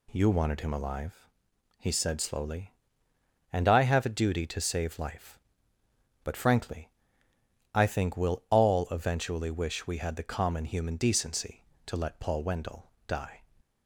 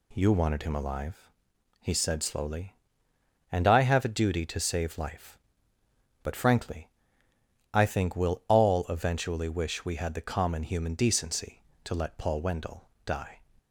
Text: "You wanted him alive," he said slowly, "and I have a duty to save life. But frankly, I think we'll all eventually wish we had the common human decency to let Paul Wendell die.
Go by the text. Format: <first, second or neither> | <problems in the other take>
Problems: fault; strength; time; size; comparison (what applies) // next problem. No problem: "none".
neither | pauses between "Wendell" and "die"; slight; the same in both